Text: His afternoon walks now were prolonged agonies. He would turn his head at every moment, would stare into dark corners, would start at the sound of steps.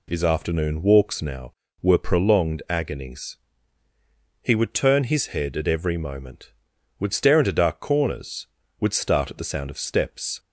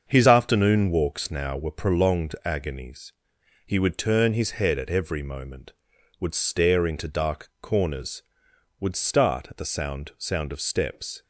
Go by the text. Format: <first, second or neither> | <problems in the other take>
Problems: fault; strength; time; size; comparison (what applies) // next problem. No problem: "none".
first | starts louder than the rest; until 1.0 s; 6.5 dB // says "sound" twice; at 10.1 s